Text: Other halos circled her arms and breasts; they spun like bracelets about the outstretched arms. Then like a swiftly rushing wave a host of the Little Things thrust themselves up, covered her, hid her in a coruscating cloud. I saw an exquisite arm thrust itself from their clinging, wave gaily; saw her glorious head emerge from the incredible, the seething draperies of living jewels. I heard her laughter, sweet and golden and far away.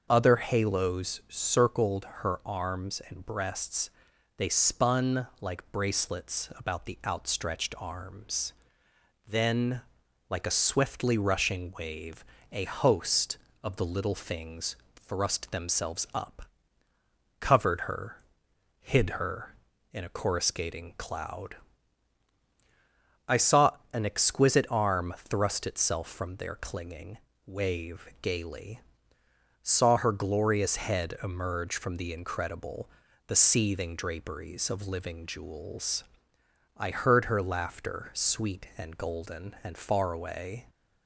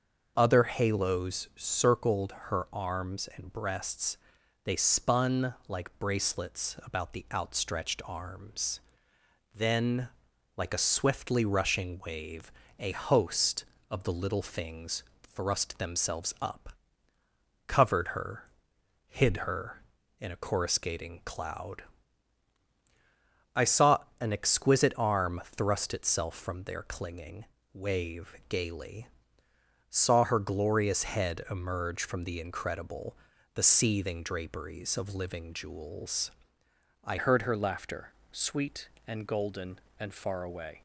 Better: first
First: starts louder than the rest; until 1.1 s; 6.5 dB // pauses between "circled" and "her"; slight; at 2.0 s; 0.16 s long // pauses between "spun" and "like"; slight; at 5.2 s; 0.16 s long // pauses between "Then" and "like"; noticeable; at 9.8 s; 0.48 s long // pauses between "wave" and "a"; slight; at 12.2 s; 0.26 s long // pauses between "Things" and "thrust"; slight; at 14.7 s; 0.18 s long // pauses between "saw" and "an"; slight; at 23.7 s; 0.20 s long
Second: starts louder than the rest; until 1.3 s; 6.5 dB // pauses between "circled" and "her"; slight; at 2.3 s; 0.16 s long // pauses between "spun" and "like"; slight; at 5.5 s; 0.16 s long // pauses between "Then" and "like"; noticeable; at 10.0 s; 0.48 s long // pauses between "wave" and "a"; slight; at 12.5 s; 0.26 s long // pauses between "Things" and "thrust"; slight; at 15.0 s; 0.18 s long // pauses between "saw" and "an"; slight; at 23.9 s; 0.20 s long // changes voice at "heard"; from 37.1 s on; 3.7 s long

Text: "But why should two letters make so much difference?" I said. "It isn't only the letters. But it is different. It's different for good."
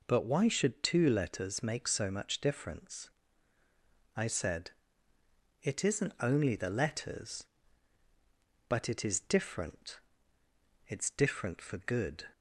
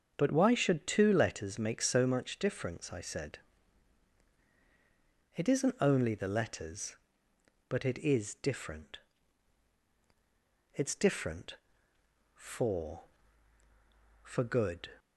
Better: first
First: none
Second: starts louder than the rest; until 1.1 s; 6.5 dB // says "for" twice; at 14.2 s

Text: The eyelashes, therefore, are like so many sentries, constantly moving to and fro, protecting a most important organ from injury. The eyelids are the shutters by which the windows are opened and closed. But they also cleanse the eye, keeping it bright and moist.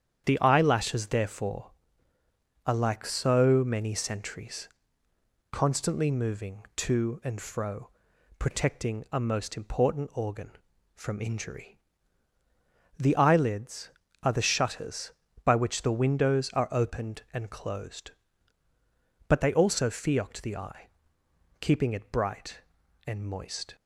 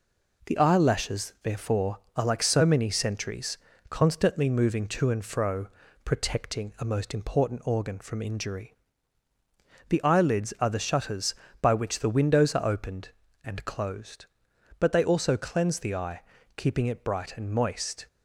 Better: second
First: starts louder than the rest; strong; until 1.2 s; 8.5 dB // says "fiocked" for "cleanse"; at 19.9 s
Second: none

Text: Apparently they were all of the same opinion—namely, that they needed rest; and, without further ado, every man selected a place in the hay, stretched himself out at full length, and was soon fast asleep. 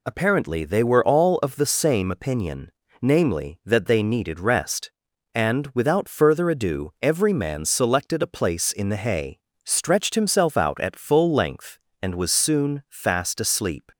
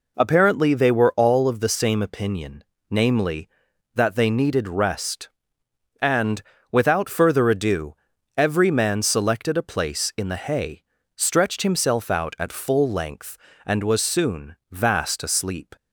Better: first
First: none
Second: says "vast" for "fast"; at 14.7 s

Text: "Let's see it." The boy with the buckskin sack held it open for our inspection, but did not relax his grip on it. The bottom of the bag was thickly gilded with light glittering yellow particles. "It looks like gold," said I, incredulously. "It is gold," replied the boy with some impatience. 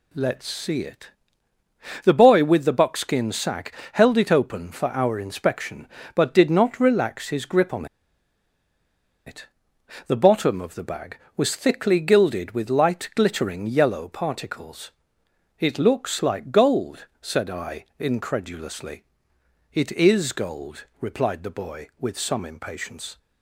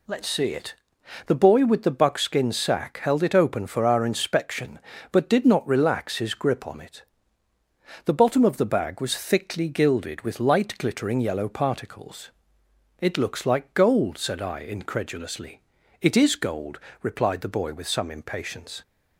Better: second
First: pauses between "sack" and "held"; slight; at 3.7 s; 0.22 s long // pauses between "on" and "it"; strong; at 7.8 s; 1.4 s long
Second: none

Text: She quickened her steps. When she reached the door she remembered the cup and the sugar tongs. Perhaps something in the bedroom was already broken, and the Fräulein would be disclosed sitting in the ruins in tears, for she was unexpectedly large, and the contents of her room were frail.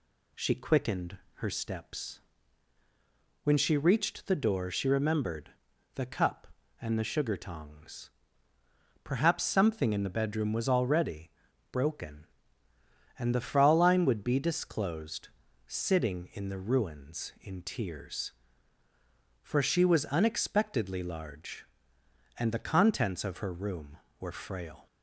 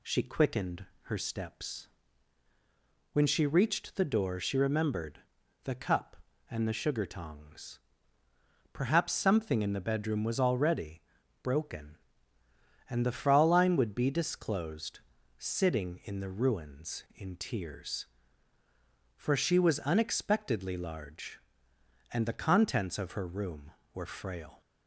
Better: neither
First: pauses between "quickened" and "her"; slight; at 1.1 s; 0.18 s long // pauses between "remembered" and "the"; at 5.5 s; 0.44 s long // pauses between "already" and "broken"; at 11.3 s; 0.42 s long // pauses between "disclosed" and "sitting"; at 15.2 s; 0.38 s long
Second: pauses between "quickened" and "her"; slight; at 0.8 s; 0.18 s long // pauses between "remembered" and "the"; at 5.1 s; 0.44 s long // pauses between "already" and "broken"; at 11.0 s; 0.42 s long // pauses between "disclosed" and "sitting"; at 14.9 s; 0.38 s long

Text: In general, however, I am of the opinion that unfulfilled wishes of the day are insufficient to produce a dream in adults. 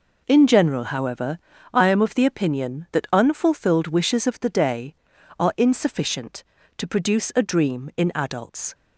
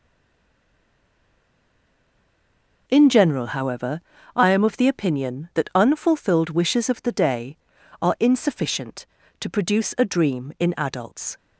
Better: first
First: none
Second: stays silent before the first word; strong; until 2.8 s; 2.8 s long

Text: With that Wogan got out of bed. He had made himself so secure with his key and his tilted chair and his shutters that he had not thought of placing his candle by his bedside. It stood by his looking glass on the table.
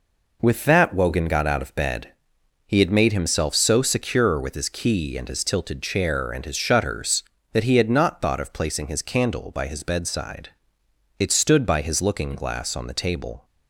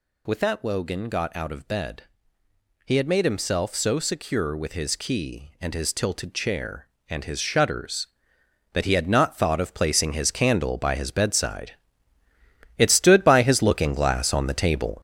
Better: first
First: none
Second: gets louder; strong; throughout; 7.5 dB

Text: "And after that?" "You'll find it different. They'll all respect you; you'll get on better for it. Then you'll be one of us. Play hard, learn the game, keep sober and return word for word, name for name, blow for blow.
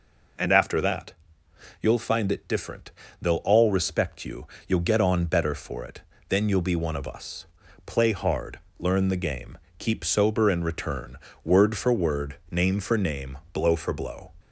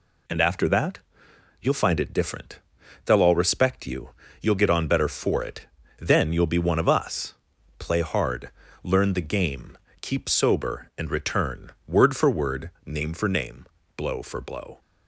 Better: neither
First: pauses between "return" and "word"; slight; at 11.1 s; 0.26 s long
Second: pauses between "return" and "word"; slight; at 11.7 s; 0.16 s long

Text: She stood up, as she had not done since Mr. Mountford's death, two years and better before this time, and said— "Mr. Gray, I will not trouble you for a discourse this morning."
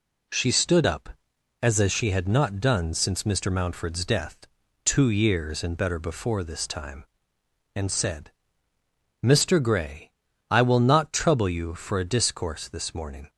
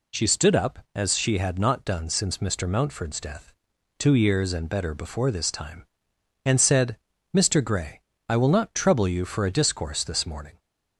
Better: second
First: says "as" twice; at 1.7 s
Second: none

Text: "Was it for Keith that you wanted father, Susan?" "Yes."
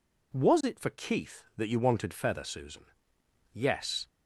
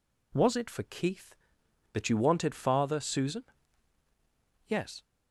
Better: second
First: says "feather" for "father"; at 2.1 s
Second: none

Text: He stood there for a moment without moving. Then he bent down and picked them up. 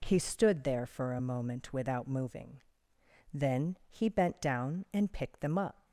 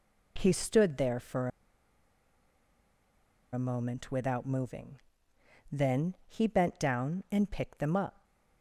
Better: first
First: none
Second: pauses between "for" and "a"; strong; at 1.4 s; 2.0 s long

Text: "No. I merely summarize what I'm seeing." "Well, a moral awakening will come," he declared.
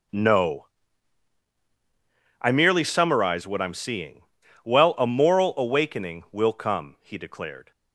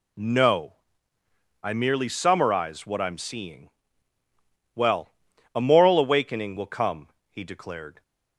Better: neither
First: none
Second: none

